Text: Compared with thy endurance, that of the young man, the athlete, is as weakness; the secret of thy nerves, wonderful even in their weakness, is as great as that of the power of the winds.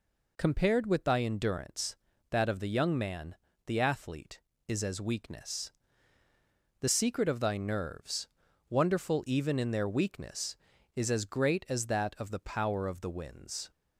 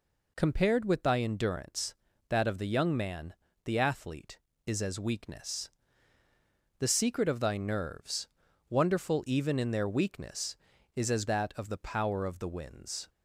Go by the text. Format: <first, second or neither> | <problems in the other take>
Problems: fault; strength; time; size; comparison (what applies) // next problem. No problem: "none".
first | skips "great as"; at 11.2 s